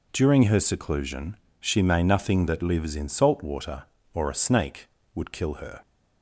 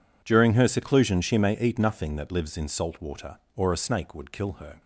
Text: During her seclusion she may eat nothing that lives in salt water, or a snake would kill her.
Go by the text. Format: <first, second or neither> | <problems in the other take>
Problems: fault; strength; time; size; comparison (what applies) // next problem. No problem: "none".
second | pauses between "seclusion" and "she"; slight; at 1.3 s; 0.22 s long // skips "eat"; at 2.0 s